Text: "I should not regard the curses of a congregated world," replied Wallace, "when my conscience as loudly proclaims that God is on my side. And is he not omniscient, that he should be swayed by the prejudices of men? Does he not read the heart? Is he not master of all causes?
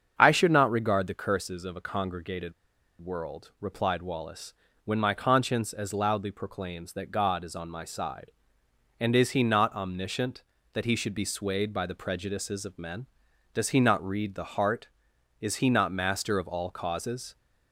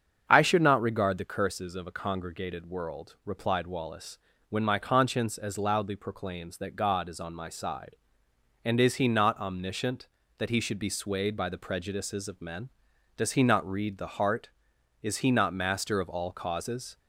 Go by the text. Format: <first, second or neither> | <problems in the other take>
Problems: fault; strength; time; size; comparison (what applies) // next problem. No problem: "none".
second | starts louder than the rest; until 1.1 s; 7 dB; also in the second // pauses between "congregated" and "world"; noticeable; at 2.5 s; 0.47 s long